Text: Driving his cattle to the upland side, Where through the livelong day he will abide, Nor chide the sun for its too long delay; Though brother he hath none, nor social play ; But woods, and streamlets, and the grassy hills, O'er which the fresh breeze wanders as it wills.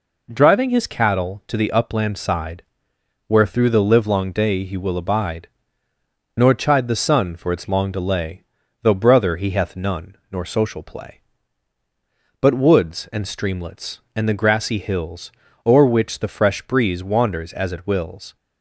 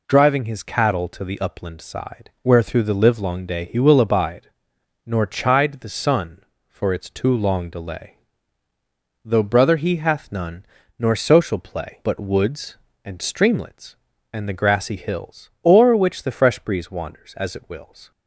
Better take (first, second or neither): second